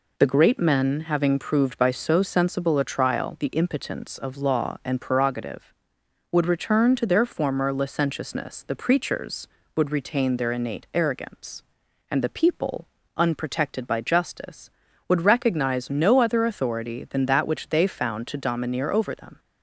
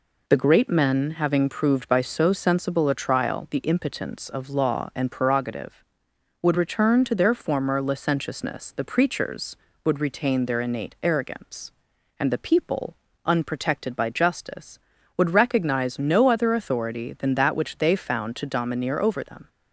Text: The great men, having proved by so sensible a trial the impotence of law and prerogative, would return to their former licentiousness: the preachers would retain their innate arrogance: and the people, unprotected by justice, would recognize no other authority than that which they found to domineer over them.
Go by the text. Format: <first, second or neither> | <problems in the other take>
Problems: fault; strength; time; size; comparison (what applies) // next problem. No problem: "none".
neither | none